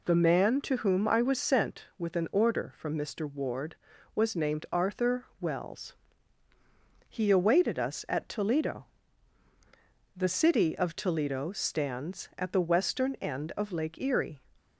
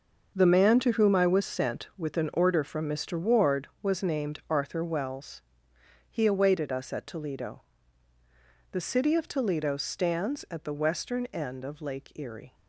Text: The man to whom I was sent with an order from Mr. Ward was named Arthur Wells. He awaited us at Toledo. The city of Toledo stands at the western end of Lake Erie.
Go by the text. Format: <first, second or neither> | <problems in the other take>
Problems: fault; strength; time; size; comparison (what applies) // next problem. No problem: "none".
first | gets quieter; strong; throughout; 11 dB